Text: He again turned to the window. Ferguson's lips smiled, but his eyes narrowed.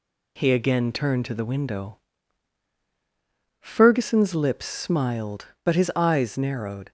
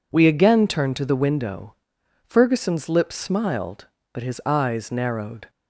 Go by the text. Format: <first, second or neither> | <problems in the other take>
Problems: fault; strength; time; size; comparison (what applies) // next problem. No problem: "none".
first | says "We" for "He"; at 0.1 s